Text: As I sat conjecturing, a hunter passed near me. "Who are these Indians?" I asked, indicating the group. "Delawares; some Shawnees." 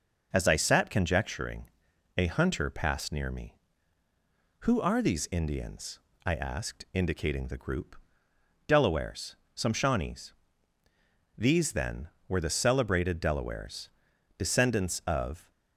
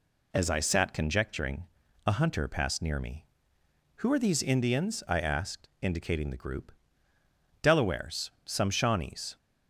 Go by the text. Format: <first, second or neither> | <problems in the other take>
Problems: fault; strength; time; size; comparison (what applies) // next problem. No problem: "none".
second | goes on to say "These then were the celebrated Delawares descendants of"; strong; from 11.3 s on; 4.1 s long